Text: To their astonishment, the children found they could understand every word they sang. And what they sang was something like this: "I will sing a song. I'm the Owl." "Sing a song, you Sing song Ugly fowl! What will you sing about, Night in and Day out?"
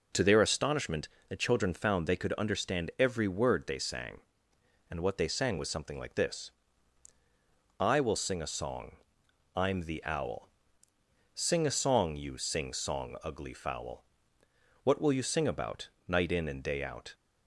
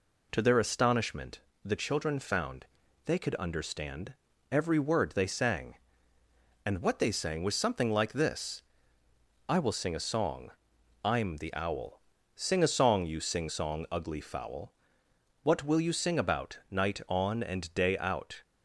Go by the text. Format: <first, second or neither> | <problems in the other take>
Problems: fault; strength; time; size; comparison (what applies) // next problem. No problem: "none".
first | pauses between "found" and "they"; at 2.6 s; 0.40 s long // pauses between "understand" and "every"; at 4.1 s; 0.38 s long // says "on" for "in"; at 17.0 s